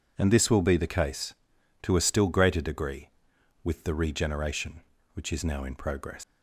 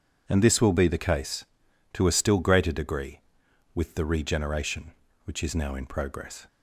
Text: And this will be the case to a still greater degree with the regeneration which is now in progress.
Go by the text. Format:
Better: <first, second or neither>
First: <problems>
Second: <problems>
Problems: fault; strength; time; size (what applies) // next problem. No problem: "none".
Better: second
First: leaves "progress" unfinished; at 6.2 s; 120 ms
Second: none